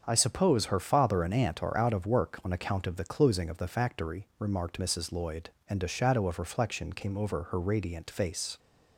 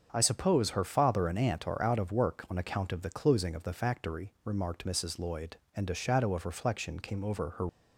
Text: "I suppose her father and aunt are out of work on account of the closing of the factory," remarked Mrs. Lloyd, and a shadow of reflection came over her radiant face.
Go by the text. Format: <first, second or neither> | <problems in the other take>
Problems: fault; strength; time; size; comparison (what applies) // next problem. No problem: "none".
first | starts louder than the rest; until 1.1 s; 6.5 dB; also in the first // stops before "radiant face"; at 7.6 s